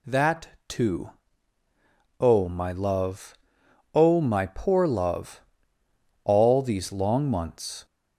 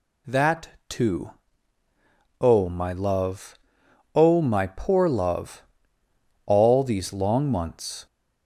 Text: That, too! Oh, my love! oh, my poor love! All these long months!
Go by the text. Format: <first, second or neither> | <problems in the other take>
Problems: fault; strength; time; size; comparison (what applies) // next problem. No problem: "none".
neither | none